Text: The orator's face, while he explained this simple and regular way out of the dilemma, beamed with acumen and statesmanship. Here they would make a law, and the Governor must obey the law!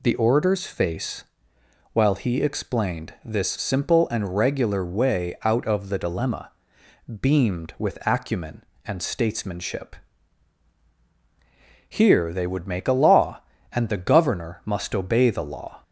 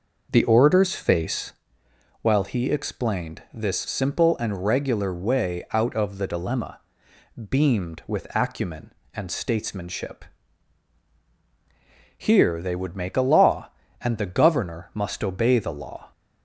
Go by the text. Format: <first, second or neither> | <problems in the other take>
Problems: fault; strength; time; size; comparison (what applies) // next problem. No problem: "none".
first | starts louder than the rest; noticeable; until 1.6 s; 5.5 dB